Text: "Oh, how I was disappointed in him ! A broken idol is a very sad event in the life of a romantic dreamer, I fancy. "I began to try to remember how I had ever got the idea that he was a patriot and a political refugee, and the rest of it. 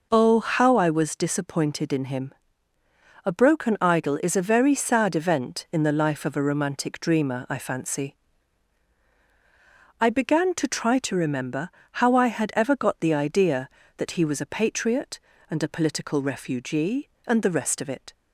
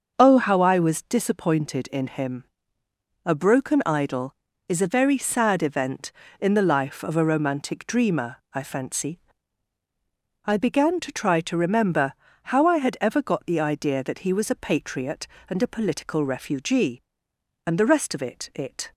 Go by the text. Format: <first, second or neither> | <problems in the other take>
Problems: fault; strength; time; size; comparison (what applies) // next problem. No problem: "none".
first | starts louder than the rest; until 1.1 s; 6.5 dB // pauses between "remember" and "how"; slight; at 12.1 s; 0.30 s long; slight in the first // says "it" twice; at 18.5 s